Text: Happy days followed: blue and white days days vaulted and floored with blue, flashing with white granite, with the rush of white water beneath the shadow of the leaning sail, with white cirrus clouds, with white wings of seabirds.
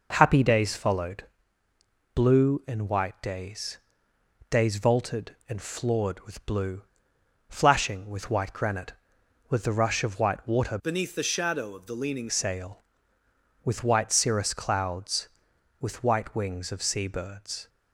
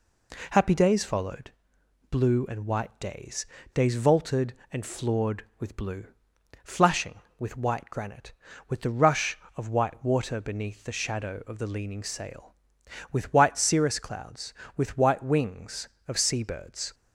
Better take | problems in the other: second | pauses between "days" and "days"; noticeable; at 3.7 s; 0.72 s long; slight in the second // changes voice from "beneath" to "leaning"; from 10.8 to 12.2 s; 1.4 s long

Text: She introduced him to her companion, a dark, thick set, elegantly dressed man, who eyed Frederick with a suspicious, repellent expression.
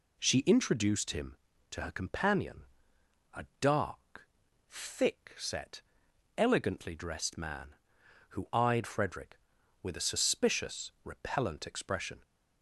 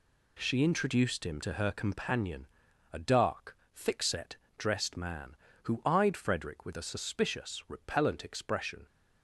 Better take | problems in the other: first | skips "elegantly"; at 4.4 s

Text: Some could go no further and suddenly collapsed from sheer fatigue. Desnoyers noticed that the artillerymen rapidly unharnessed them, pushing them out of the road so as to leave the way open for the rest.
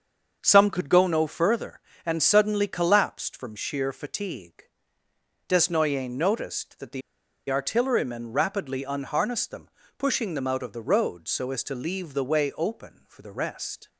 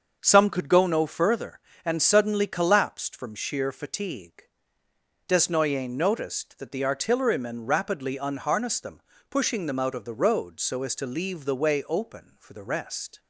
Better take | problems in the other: second | starts louder than the rest; until 1.4 s; 6.5 dB; also in the second // pauses between "the" and "artillerymen"; noticeable; at 7.0 s; 0.48 s long

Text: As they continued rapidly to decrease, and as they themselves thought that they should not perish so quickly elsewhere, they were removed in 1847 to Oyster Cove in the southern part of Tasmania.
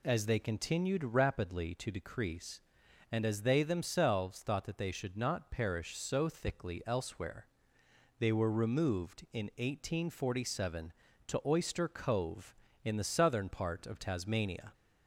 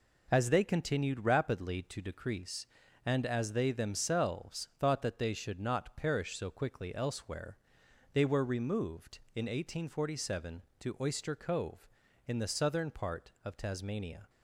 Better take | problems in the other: second | says "thickly" for "quickly"; at 6.2 s

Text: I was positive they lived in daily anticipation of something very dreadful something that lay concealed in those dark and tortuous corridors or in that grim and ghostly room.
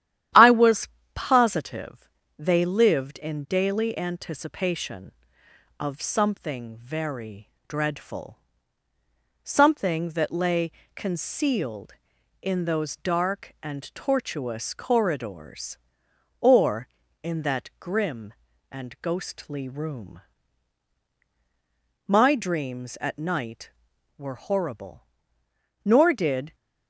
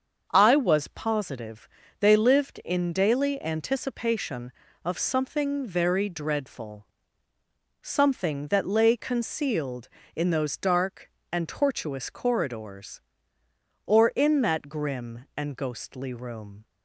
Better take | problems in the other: second | starts louder than the rest; strong; until 1.5 s; 11.5 dB; also in the second // pauses between "was" and "positive"; slight; at 0.8 s; 0.24 s long // pauses between "positive" and "they"; slight; at 2.0 s; 0.30 s long; slight in the second // pauses between "very" and "dreadful"; slight; at 7.5 s; 0.18 s long // pauses between "dreadful" and "something"; at 8.3 s; 1.0 s long; noticeable in the second // pauses between "lay" and "concealed"; slight; at 10.7 s; 0.24 s long // goes on to say "My dreams at night were horrible nor did"; strong; from 22.0 s on; 4.4 s long

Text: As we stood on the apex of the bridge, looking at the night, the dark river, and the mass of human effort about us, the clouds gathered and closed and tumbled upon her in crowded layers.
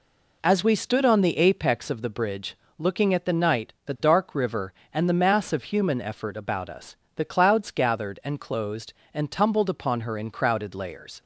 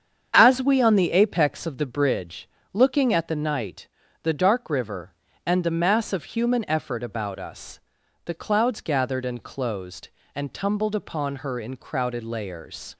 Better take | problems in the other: first | starts louder than the rest; strong; until 1.3 s; 7.5 dB // skips "stood"; at 0.8 s

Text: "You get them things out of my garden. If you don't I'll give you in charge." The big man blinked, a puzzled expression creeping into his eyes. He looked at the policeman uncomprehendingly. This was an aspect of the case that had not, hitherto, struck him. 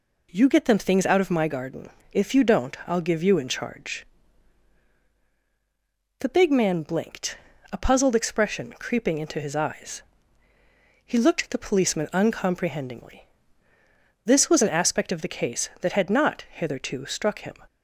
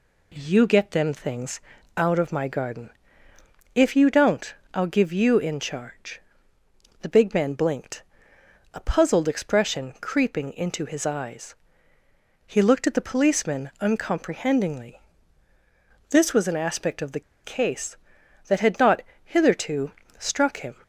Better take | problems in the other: first | pauses between "things" and "out"; slight; at 1.6 s; 0.34 s long // pauses between "don't" and "I'll"; slight; at 4.5 s; 0.18 s long // pauses between "the" and "case"; slight; at 17.2 s; 0.23 s long

